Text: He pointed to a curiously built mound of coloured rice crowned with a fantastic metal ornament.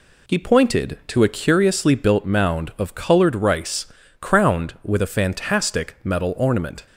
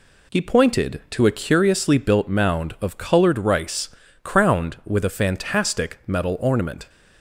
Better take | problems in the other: neither | pauses between "rice" and "crowned"; slight; the same in both

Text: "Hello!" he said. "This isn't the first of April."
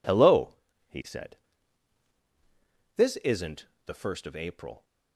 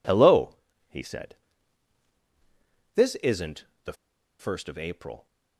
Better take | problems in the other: first | pauses between "isn't" and "the"; slight; at 3.6 s; 0.20 s long; slight in the first // pauses between "the" and "first"; at 3.9 s; 0.45 s long

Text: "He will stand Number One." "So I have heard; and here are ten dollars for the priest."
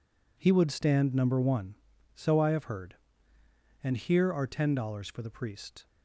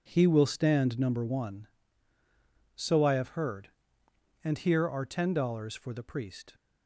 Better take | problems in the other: second | says "would" for "will"; at 0.5 s

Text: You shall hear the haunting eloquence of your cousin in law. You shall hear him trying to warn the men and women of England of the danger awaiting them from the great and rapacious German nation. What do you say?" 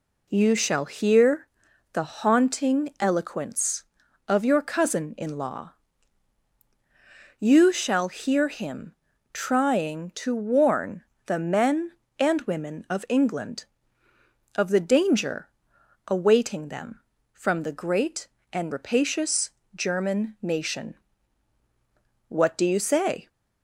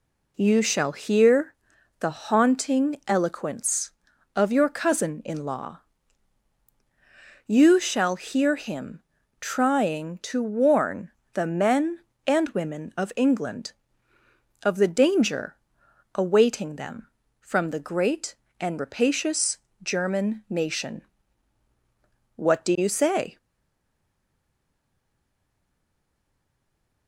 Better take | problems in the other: first | pauses between "hear" and "the"; noticeable; at 1.5 s; 0.46 s long; noticeable in the first // pauses between "him" and "trying"; at 9.0 s; 0.38 s long; also in the first // pauses between "warn" and "the"; slight; at 11.0 s; 0.24 s long; slight in the first // pauses between "danger" and "awaiting"; noticeable; at 15.5 s; 0.60 s long; noticeable in the first // pauses between "rapacious" and "German"; slight; at 19.5 s; 0.24 s long; slight in the first // stays silent after the last word; strong; from 23.3 s on; 3.7 s long

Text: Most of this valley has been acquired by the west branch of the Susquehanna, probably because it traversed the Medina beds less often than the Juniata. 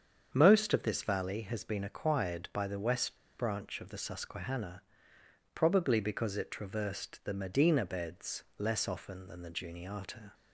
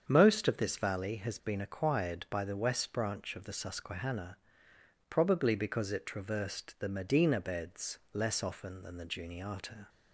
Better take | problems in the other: second | starts louder than the rest; strong; until 1.3 s; 7.5 dB; strong in the second // pauses between "west" and "branch"; slight; at 3.1 s; 0.23 s long

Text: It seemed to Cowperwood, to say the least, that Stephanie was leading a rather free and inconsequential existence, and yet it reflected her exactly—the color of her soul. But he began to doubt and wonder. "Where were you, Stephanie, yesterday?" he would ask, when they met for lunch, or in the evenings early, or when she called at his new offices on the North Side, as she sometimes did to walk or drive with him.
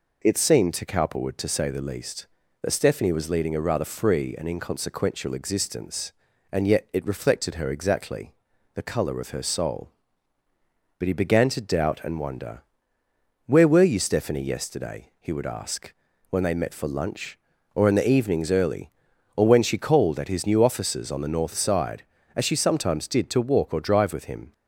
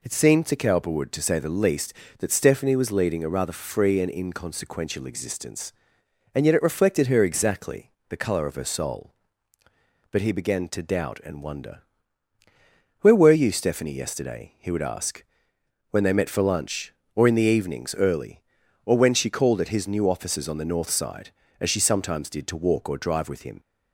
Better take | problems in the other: neither | none

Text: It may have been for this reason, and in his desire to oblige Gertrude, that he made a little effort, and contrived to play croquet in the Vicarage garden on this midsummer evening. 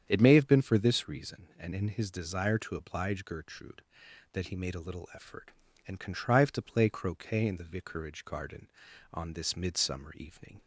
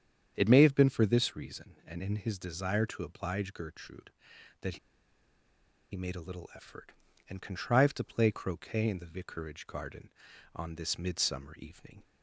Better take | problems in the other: first | starts louder than the rest; strong; until 1.3 s; 8.5 dB; strong in the first // pauses between "that" and "he"; at 4.7 s; 1.1 s long

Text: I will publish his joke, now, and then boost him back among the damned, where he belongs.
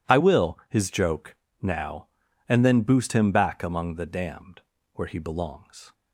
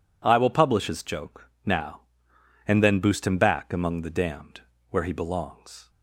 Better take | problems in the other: second | skips "publish"; at 0.6 s

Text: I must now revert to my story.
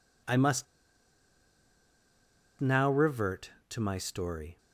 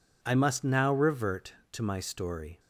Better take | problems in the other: second | pauses between "must" and "now"; strong; at 0.6 s; 1.9 s long

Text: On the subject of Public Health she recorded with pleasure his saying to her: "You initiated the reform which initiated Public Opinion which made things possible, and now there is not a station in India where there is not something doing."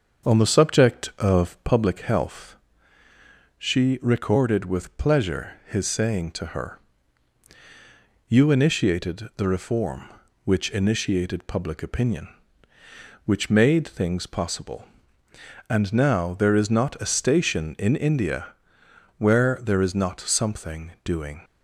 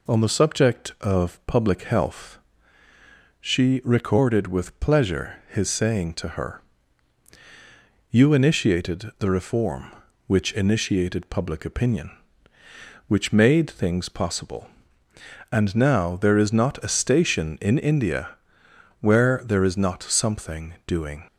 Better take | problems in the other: second | starts louder than the rest; until 1.9 s; 6.5 dB // pauses between "Health" and "she"; at 2.5 s; 1.0 s long; also in the second // pauses between "India" and "where"; noticeable; at 18.5 s; 0.64 s long; noticeable in the second

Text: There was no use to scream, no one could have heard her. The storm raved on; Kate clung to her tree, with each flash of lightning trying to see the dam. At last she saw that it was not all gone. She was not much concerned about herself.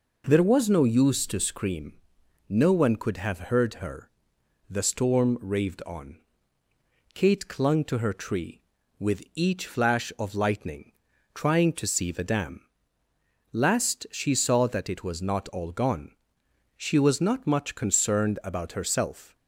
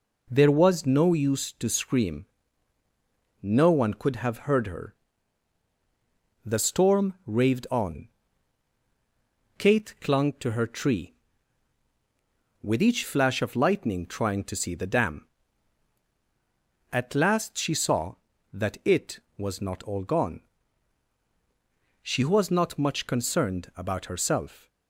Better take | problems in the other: second | pauses between "lightning" and "trying"; at 10.9 s; 0.42 s long // skips "At"; at 13.0 s

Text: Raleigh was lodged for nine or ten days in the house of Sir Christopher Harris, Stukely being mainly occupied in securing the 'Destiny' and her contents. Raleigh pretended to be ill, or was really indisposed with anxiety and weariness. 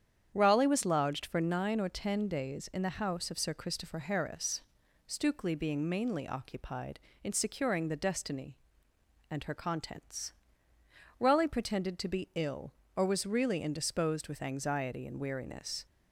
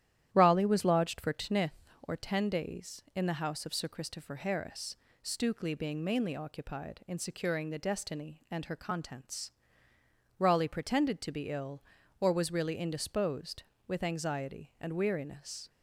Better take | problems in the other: first | starts louder than the rest; strong; until 1.3 s; 11.5 dB; strong in the first // says "tnith" for "nine"; at 1.3 s

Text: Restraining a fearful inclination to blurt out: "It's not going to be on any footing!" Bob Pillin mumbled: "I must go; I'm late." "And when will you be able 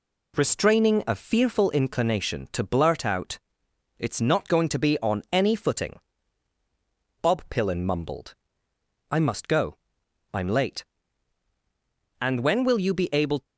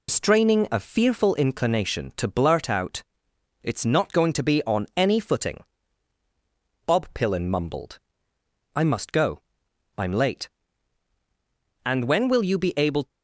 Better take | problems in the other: first | loses the start of "Restraining"; at 0.0 s; 105 ms

